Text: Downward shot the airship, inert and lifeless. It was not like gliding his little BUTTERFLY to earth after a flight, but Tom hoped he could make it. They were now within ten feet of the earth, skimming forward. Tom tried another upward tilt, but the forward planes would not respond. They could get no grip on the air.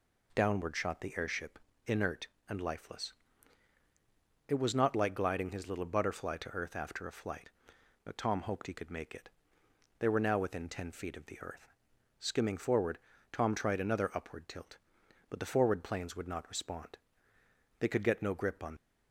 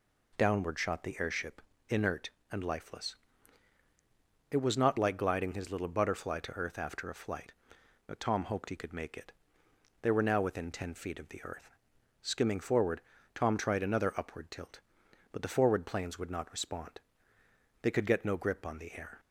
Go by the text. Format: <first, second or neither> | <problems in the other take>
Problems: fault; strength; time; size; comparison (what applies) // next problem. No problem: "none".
second | stops before "the air"; at 18.7 s